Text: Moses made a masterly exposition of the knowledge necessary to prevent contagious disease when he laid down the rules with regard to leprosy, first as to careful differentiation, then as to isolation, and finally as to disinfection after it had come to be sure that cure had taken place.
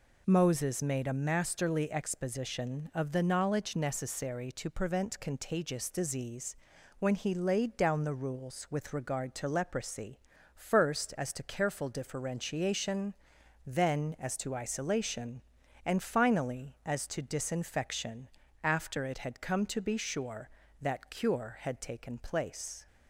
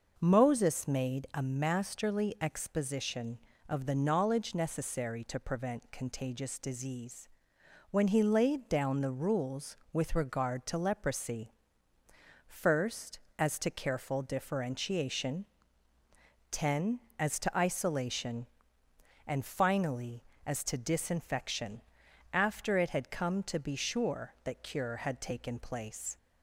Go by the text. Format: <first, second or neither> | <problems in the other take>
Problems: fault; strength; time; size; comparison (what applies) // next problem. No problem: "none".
first | pauses between "disease" and "when"; noticeable; at 7.2 s; 0.62 s long; noticeable in the first // says "ten" for "then"; at 16.4 s // pauses between "disinfection" and "after"; noticeable; at 21.8 s; 0.52 s long; slight in the first